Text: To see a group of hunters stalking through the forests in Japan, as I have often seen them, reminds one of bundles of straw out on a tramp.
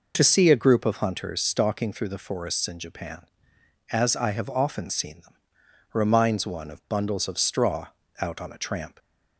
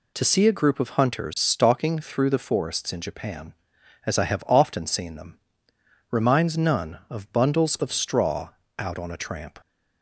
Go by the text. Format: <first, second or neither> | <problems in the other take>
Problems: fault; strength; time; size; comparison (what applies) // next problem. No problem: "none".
first | says "none" for "one"; at 6.5 s // pauses between "straw" and "out"; slight; at 8.4 s; 0.28 s long; slight in the first